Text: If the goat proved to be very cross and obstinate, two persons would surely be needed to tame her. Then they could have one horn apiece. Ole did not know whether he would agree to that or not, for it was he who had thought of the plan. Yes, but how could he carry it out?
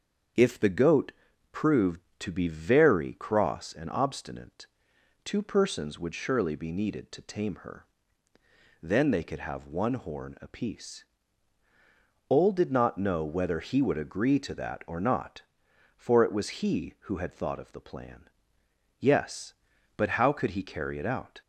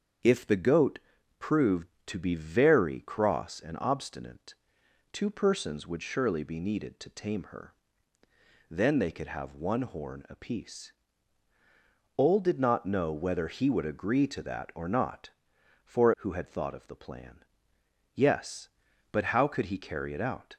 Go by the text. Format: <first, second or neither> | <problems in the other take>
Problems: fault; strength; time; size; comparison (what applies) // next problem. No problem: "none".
first | starts louder than the rest; until 1.6 s; 7 dB; also in the first // pauses between "goat" and "proved"; at 0.9 s; 0.40 s long; also in the first // skips "it was he"; at 16.1 s